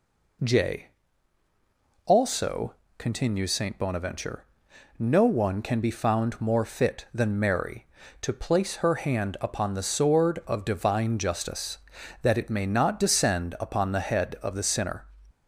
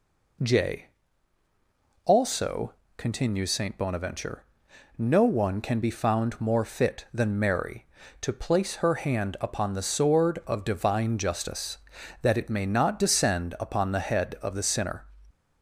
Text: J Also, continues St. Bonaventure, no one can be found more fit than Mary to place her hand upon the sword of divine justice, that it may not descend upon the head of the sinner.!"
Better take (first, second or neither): neither